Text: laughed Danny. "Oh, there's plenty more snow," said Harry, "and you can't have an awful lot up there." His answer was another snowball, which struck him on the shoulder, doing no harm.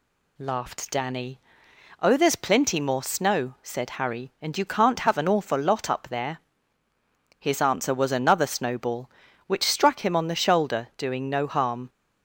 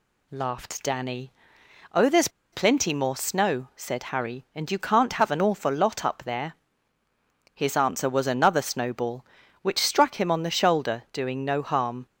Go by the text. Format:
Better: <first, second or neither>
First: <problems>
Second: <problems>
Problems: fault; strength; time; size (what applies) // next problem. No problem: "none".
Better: first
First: none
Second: pauses between "there's" and "plenty"; slight; at 2.2 s; 0.24 s long